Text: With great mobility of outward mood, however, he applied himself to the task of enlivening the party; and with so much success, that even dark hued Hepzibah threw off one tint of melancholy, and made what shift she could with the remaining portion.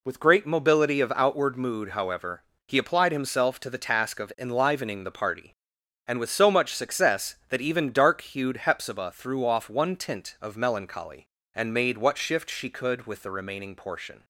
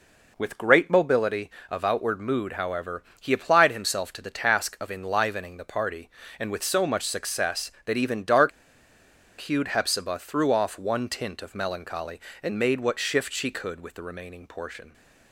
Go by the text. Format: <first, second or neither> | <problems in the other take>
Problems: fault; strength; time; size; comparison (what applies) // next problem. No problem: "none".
first | pauses between "dark" and "hued"; noticeable; at 8.5 s; 0.90 s long